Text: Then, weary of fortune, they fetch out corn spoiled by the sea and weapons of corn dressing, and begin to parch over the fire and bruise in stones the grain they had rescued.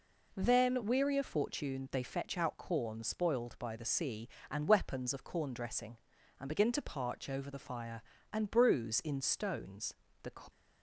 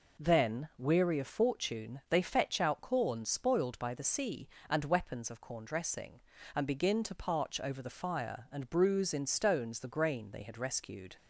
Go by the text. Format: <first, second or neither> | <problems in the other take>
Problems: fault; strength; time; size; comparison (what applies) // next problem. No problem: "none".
second | pauses between "stones" and "the"; slight; at 9.9 s; 0.28 s long // stops before "grain they had rescued"; at 10.4 s